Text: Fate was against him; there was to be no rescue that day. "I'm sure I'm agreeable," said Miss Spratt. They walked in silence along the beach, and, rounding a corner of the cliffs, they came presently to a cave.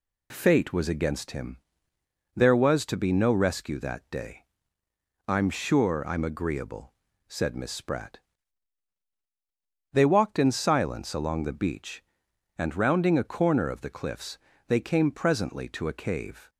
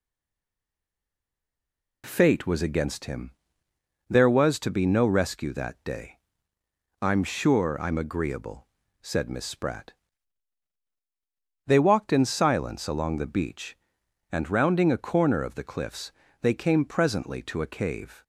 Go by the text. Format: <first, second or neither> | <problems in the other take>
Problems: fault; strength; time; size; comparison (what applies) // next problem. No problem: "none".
first | stays silent before the first word; noticeable; until 2.0 s; 2.0 s long